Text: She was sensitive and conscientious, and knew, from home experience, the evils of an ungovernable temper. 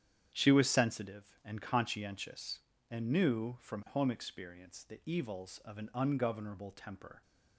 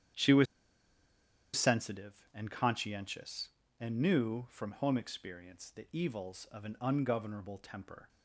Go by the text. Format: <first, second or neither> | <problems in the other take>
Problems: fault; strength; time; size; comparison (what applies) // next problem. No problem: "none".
first | starts louder than the rest; strong; until 2.2 s; 9 dB; strong in the first // pauses between "was" and "sensitive"; at 0.4 s; 1.1 s long